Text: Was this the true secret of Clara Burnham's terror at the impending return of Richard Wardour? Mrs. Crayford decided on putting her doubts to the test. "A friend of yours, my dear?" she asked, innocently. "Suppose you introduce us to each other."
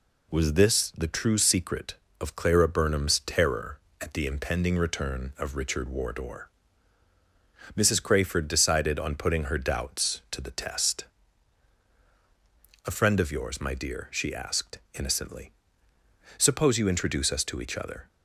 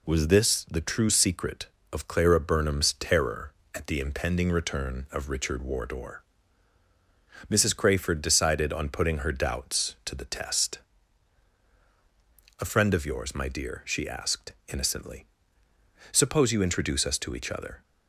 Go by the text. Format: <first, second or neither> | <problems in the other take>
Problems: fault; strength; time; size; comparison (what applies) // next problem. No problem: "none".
neither | none